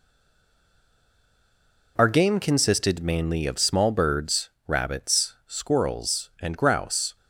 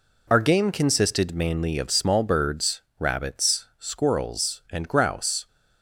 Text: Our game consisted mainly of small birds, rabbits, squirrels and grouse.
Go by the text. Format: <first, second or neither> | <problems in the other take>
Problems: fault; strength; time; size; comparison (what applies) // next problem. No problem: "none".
second | stays silent before the first word; noticeable; until 1.9 s; 1.9 s long